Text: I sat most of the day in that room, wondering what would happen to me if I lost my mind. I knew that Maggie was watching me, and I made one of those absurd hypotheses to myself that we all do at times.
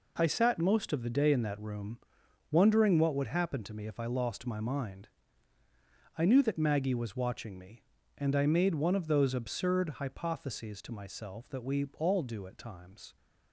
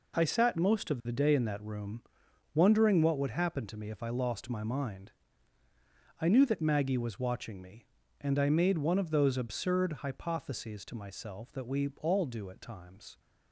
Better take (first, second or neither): neither